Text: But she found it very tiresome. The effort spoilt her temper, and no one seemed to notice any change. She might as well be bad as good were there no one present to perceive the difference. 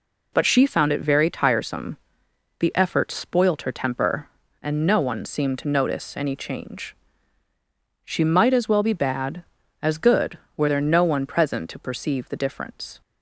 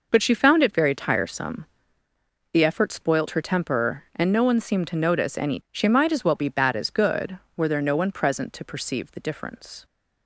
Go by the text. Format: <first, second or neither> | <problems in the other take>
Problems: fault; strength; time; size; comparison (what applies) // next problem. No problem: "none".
first | skips "change"; at 5.6 s